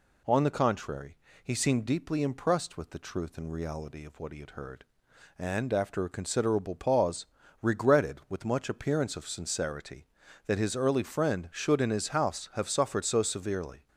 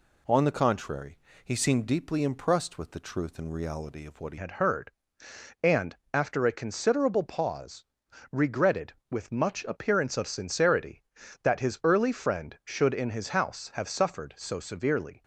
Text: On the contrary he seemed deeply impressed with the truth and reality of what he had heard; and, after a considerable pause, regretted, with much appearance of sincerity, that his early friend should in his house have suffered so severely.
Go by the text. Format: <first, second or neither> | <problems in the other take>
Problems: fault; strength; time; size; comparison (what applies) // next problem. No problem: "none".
first | pauses between "contrary" and "he"; slight; at 1.1 s; 0.26 s long; slight in the first // changes voice at "had"; from 4.3 s on; 10.9 s long